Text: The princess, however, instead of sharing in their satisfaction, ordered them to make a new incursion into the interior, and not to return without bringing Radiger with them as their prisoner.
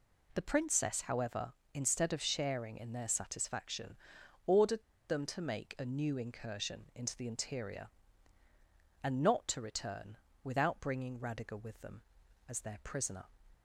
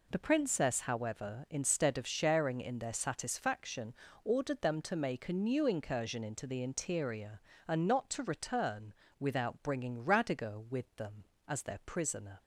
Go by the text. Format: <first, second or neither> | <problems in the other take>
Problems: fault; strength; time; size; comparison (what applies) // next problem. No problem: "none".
second | pauses between "ordered" and "them"; slight; at 4.8 s; 0.26 s long // pauses between "return" and "without"; slight; at 10.1 s; 0.28 s long; slight in the second